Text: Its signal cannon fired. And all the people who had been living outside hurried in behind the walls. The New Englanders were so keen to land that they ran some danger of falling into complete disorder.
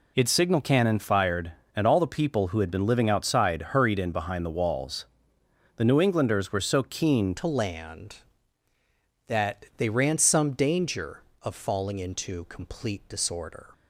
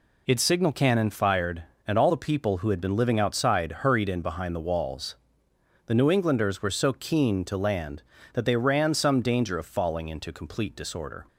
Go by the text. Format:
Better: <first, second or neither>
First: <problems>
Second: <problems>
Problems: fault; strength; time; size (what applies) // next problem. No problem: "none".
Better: second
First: changes voice at "to"; from 7.3 s on; 6.3 s long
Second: none